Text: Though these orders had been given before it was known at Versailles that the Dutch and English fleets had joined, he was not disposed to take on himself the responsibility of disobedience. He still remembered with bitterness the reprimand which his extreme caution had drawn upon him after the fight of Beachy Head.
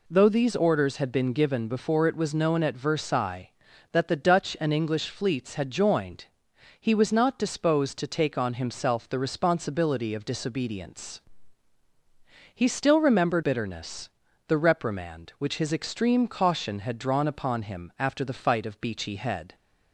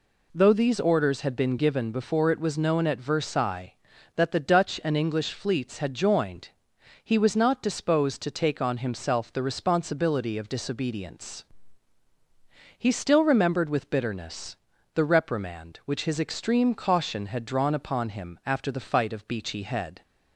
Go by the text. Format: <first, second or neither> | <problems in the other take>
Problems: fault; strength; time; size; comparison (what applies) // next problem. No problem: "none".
second | skips "with"; at 13.4 s // pauses between "bitterness" and "the"; at 14.0 s; 0.38 s long; also in the second